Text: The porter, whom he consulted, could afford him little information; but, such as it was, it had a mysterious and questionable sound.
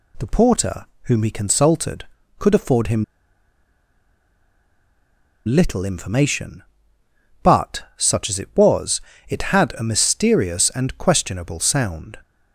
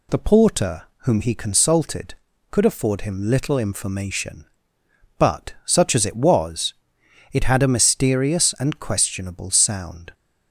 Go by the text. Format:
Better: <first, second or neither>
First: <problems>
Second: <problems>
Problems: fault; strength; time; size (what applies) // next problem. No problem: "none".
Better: second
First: pauses between "him" and "little"; strong; at 3.0 s; 2.4 s long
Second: none